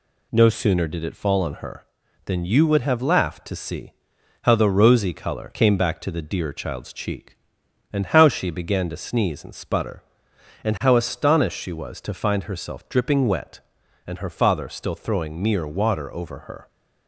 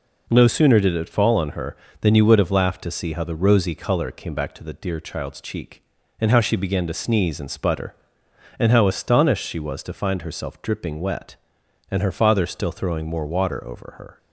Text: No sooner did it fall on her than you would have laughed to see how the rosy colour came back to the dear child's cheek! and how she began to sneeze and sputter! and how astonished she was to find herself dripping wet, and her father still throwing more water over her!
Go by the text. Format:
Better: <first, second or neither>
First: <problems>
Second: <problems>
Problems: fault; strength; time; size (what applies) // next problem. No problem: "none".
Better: second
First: pauses between "see" and "how"; noticeable; at 3.9 s; 0.50 s long // says "mere" for "more"; at 15.4 s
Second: none